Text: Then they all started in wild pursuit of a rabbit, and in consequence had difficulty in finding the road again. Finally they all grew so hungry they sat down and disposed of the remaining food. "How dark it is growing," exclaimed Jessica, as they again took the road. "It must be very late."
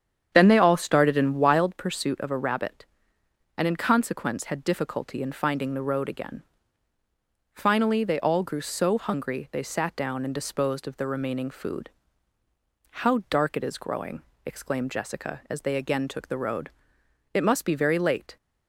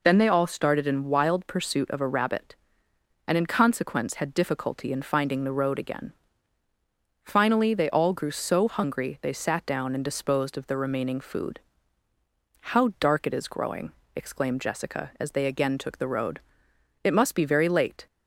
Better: second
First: starts louder than the rest; strong; until 1.7 s; 8.5 dB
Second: none

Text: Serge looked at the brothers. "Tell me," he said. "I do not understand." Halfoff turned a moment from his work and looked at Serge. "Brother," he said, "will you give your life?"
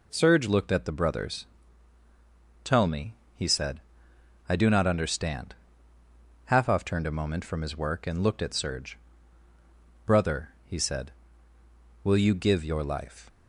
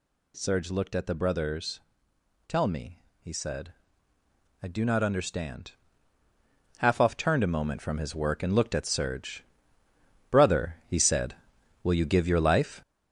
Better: first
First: none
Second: gets louder; noticeable; throughout; 6 dB

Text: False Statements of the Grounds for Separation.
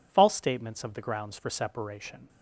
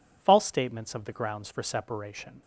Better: neither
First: none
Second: none

